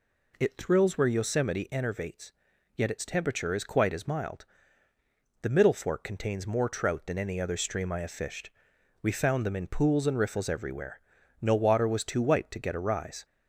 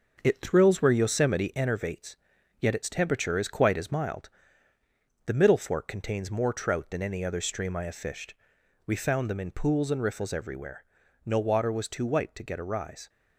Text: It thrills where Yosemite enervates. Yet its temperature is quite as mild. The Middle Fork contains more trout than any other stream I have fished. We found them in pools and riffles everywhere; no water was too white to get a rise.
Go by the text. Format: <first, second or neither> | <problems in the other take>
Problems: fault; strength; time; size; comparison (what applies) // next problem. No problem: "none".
first | gets quieter; noticeable; throughout; 4.5 dB